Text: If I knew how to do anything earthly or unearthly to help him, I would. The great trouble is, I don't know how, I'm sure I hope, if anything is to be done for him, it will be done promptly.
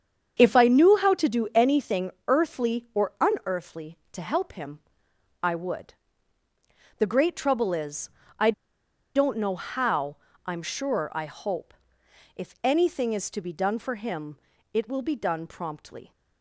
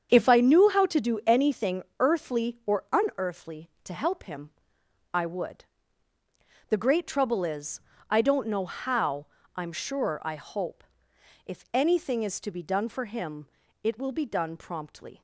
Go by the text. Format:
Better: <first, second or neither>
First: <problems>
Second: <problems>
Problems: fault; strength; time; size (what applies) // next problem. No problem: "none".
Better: second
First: starts louder than the rest; strong; until 1.3 s; 7.5 dB // pauses between "anything" and "earthly"; slight; at 2.1 s; 0.16 s long // pauses between "I" and "don't"; noticeable; at 8.5 s; 0.63 s long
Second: starts louder than the rest; strong; until 1.1 s; 7.5 dB // pauses between "anything" and "earthly"; slight; at 1.8 s; 0.16 s long